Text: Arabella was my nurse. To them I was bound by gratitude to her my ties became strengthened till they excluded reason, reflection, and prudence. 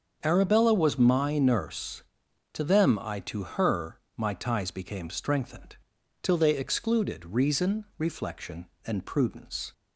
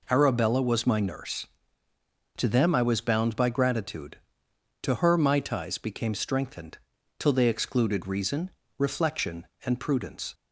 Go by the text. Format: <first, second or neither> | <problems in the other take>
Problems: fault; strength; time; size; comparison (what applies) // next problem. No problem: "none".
second | starts louder than the rest; until 1.2 s; 7 dB // skips "was bound by gratitude"; at 3.2 s // pauses between "her" and "my"; slight; at 3.9 s; 0.22 s long // pauses between "strengthened" and "till"; at 5.7 s; 0.44 s long; also in the second